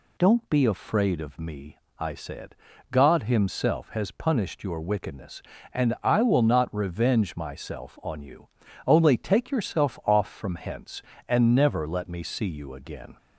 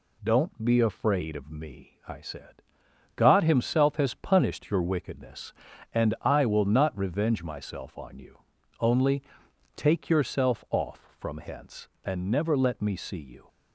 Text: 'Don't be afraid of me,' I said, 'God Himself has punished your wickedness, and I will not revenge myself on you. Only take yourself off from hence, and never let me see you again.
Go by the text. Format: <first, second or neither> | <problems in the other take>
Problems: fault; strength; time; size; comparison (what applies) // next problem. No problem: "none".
first | pauses between "Only" and "take"; noticeable; at 9.2 s; 0.54 s long // stops before "again"; at 13.4 s